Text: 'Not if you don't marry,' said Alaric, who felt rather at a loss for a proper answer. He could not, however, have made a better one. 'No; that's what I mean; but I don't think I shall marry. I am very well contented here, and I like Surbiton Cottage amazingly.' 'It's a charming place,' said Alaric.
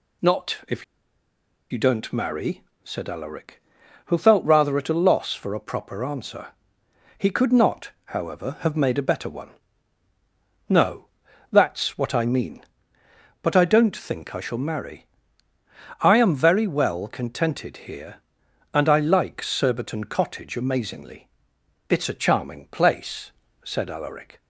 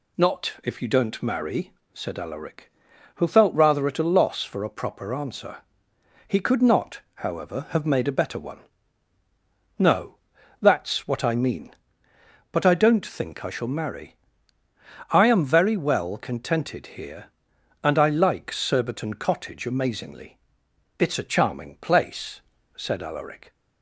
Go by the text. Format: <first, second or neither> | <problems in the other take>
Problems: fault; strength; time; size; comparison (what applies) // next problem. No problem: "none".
second | pauses between "if" and "you"; noticeable; at 0.8 s; 0.86 s long